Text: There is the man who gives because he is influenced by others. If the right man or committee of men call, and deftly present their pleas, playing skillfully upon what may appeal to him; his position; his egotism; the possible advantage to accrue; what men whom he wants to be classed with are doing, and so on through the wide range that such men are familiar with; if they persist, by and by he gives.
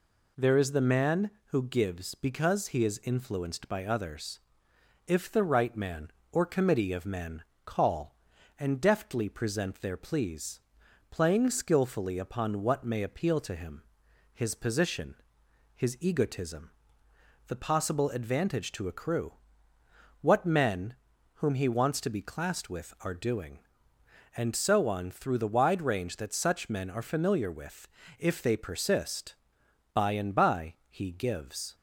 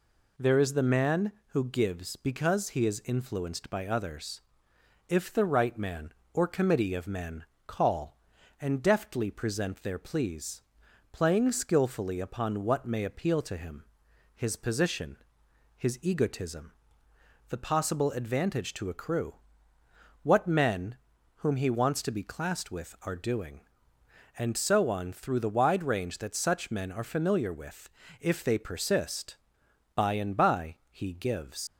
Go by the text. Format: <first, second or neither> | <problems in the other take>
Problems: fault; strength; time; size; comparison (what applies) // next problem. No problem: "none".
first | pauses between "men" and "call"; slight; at 7.4 s; 0.22 s long; slight in the first // pauses between "men" and "whom"; at 20.9 s; 0.40 s long; also in the first // leaves "gives" unfinished; at 31.6 s; 90 ms